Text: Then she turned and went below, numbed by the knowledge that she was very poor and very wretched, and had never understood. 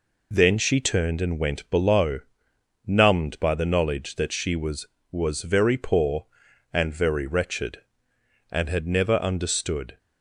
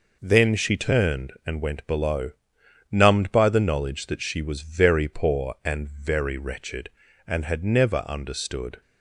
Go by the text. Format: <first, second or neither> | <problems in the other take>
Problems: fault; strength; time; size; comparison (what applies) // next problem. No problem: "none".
second | says "was" twice; at 5.0 s